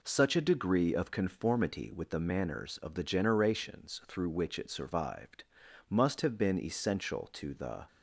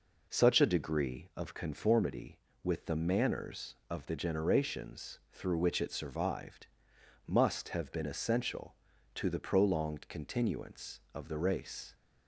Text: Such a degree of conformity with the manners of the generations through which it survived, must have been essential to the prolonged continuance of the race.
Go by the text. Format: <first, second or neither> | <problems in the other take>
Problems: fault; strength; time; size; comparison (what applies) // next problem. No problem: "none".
second | stops before "prolonged continuance of the race"; at 7.8 s